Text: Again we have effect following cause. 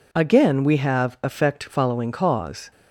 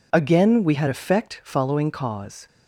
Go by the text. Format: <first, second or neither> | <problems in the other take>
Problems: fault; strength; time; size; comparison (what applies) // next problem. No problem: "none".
first | says "had" for "have"; at 0.7 s